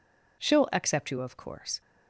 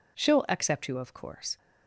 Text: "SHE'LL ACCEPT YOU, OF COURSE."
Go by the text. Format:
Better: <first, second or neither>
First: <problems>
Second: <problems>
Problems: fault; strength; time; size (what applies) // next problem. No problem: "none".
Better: neither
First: none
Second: none